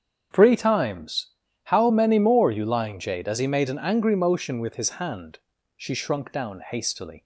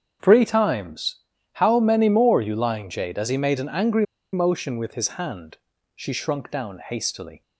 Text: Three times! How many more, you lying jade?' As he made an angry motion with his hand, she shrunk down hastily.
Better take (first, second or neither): first